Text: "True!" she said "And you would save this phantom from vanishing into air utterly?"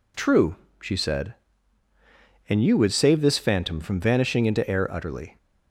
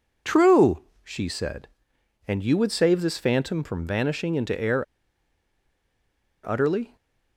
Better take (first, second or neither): first